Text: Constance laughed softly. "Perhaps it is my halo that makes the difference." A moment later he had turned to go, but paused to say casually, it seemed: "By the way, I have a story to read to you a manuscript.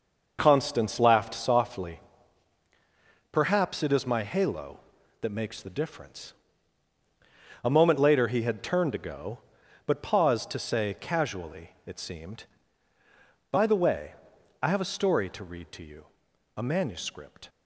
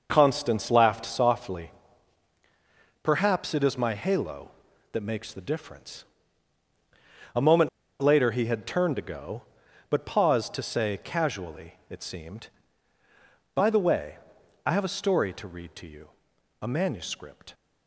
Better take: first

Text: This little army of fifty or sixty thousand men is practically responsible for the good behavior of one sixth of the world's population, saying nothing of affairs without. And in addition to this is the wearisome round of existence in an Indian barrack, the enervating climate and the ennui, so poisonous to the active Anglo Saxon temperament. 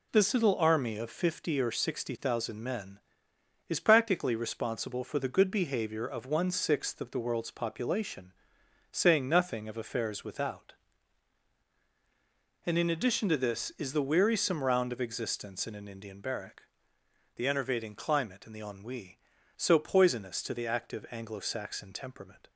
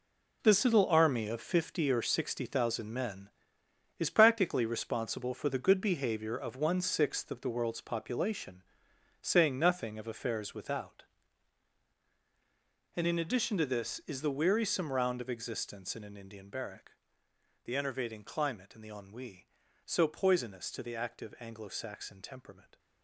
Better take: first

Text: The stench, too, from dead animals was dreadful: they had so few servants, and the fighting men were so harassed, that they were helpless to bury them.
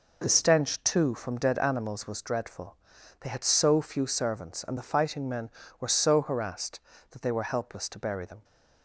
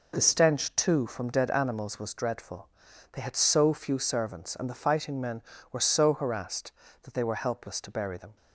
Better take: neither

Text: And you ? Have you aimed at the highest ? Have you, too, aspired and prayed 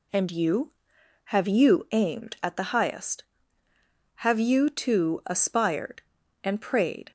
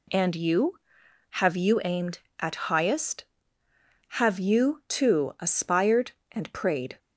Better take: first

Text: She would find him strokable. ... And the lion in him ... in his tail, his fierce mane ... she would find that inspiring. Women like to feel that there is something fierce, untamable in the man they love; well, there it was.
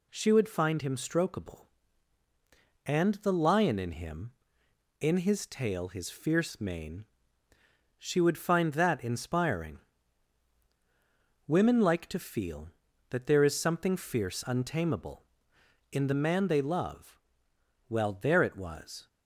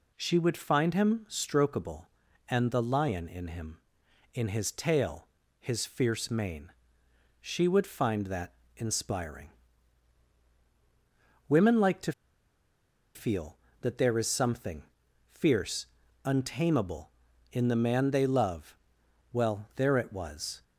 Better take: first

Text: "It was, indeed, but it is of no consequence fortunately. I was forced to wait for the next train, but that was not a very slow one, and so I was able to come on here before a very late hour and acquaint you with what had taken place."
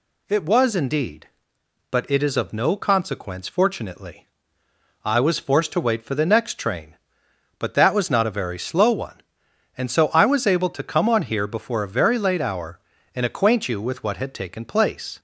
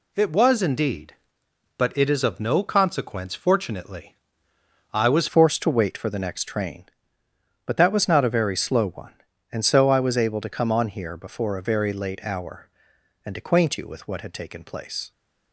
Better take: first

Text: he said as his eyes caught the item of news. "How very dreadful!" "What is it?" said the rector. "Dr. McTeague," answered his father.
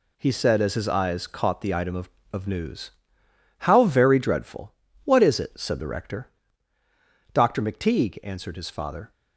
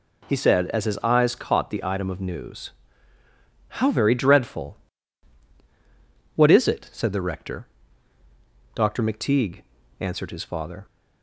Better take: second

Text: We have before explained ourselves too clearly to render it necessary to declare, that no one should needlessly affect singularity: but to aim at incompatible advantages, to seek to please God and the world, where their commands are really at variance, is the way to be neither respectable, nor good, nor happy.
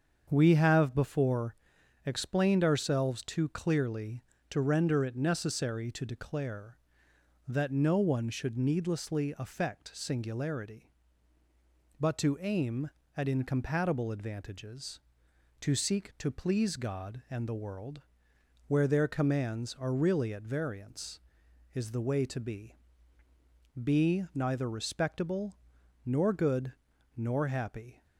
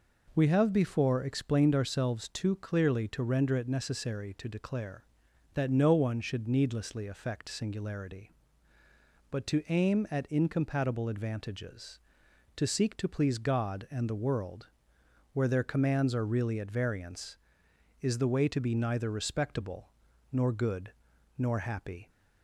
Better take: second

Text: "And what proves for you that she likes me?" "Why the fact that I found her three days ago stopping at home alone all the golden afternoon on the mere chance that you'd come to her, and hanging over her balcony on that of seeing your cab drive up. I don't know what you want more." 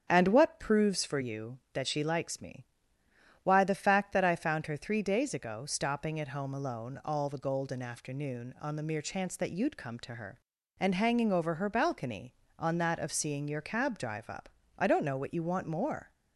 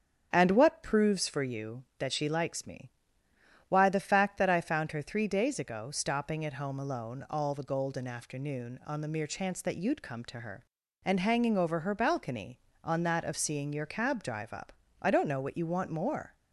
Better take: neither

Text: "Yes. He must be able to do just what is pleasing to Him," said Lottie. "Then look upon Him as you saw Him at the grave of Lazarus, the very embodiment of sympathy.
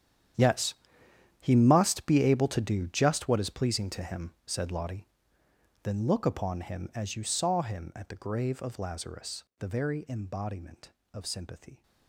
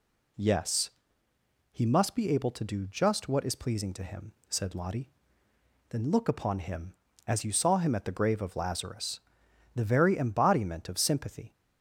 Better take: second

